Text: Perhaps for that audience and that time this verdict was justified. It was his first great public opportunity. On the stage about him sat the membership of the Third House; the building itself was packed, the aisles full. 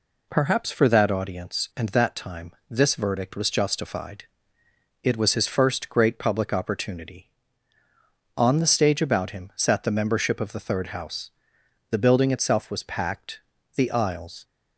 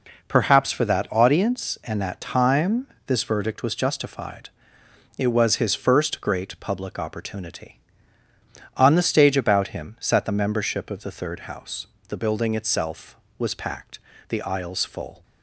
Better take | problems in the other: second | pauses between "time" and "this"; slight; at 2.5 s; 0.18 s long; slight in the second // stops before "full"; at 14.4 s

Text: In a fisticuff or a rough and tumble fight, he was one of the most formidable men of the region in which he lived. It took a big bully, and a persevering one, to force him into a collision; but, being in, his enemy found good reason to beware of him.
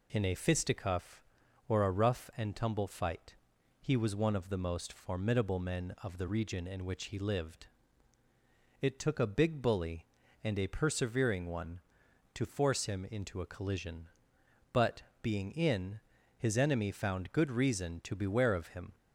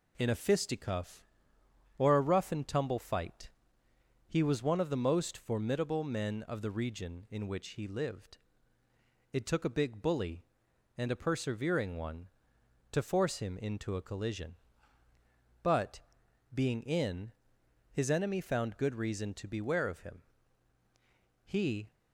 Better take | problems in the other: first | goes on to say "He"; slight; from 21.4 s on; 0.48 s long

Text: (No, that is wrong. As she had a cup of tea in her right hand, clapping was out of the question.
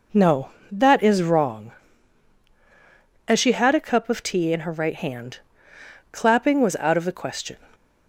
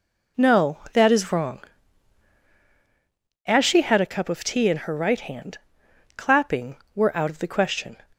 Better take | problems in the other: first | says "were" for "was"; at 6.9 s

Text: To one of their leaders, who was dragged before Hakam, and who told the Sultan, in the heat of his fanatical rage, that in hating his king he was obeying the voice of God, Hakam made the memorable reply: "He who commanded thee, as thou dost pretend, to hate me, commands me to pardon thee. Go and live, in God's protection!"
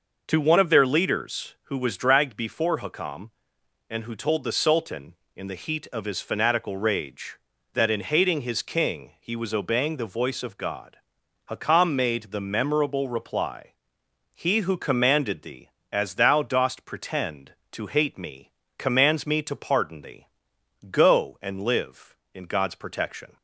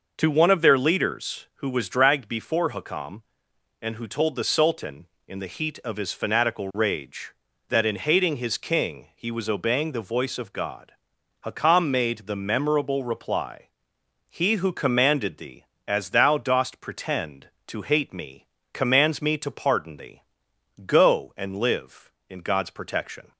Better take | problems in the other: neither | none

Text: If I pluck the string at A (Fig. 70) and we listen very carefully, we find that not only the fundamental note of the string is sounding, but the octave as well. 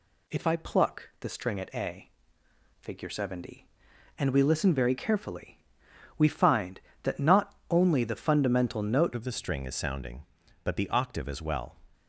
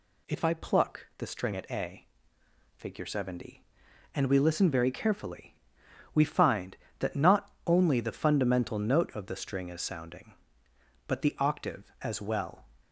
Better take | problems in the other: second | pauses between "not" and "only"; slight; at 7.5 s; 0.16 s long; slight in the second // changes voice at "of"; from 9.1 s on; 2.6 s long

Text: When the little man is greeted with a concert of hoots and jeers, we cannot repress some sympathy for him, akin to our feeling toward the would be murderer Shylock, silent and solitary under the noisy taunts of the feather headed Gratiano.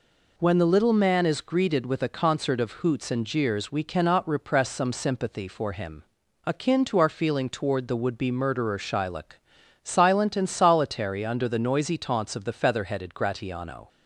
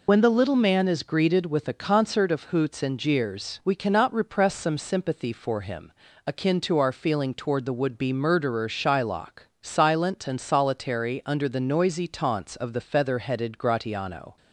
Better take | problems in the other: first | loses the start of "When"; at 0.0 s; 65 ms

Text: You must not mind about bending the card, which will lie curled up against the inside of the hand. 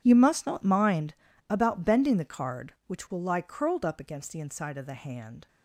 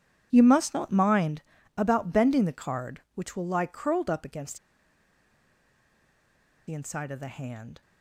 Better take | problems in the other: first | pauses between "mind" and "about"; slight; at 1.4 s; 0.34 s long; slight in the first // pauses between "against" and "the"; strong; at 4.5 s; 2.0 s long

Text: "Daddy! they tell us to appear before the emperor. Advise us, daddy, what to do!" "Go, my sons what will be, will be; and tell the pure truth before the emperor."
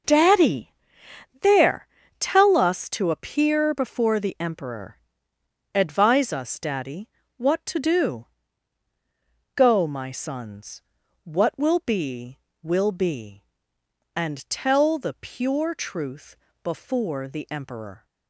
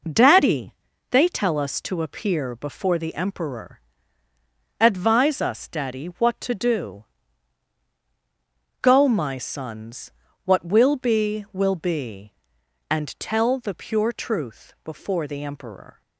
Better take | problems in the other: second | starts louder than the rest; noticeable; until 1.7 s; 6 dB // says "there" for "they"; at 1.4 s // pauses between "sons" and "what"; at 10.8 s; 0.40 s long; slight in the second // pauses between "truth" and "before"; slight; at 16.3 s; 0.26 s long

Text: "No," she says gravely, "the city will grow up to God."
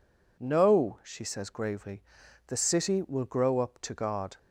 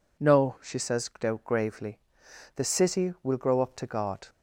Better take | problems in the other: neither | none

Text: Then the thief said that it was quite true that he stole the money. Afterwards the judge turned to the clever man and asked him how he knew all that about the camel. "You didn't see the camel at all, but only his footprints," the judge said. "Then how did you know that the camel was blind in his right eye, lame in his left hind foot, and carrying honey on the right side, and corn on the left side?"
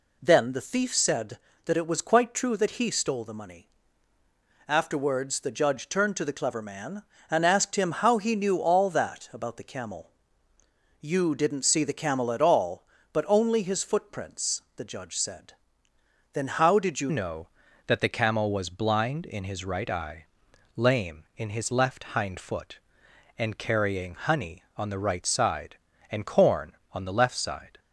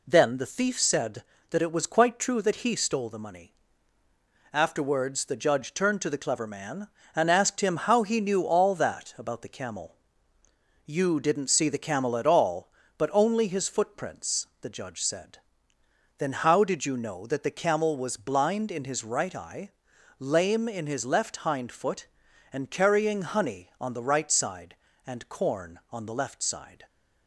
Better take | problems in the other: second | changes voice at "know"; from 17.0 s on; 10.7 s long

